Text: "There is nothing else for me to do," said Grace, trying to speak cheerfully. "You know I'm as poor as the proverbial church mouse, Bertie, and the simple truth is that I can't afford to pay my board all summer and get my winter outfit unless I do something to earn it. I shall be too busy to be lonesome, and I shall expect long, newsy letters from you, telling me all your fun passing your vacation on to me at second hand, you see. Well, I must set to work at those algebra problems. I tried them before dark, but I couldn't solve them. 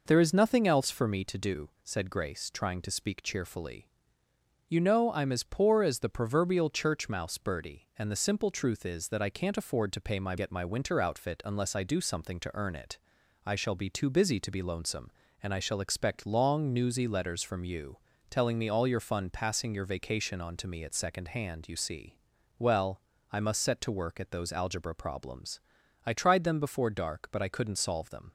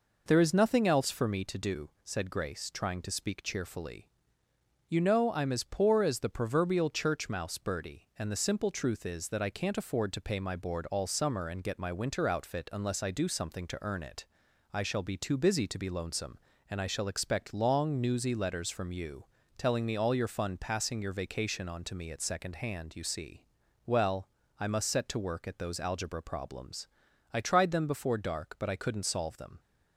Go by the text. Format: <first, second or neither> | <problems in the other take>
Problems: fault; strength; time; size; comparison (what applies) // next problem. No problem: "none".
second | skips "board all summer and"; at 10.3 s